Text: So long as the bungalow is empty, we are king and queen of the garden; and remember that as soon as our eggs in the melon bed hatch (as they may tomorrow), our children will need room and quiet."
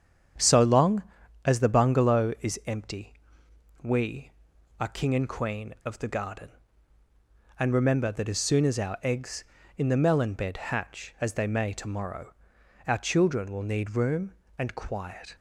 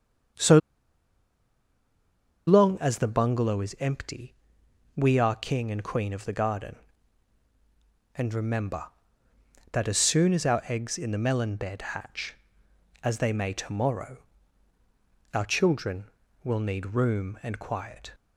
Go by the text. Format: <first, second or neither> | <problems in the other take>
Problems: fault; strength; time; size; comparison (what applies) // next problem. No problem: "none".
first | starts louder than the rest; strong; until 3.2 s; 7.5 dB; strong in the first // pauses between "So" and "long"; strong; at 0.5 s; 1.8 s long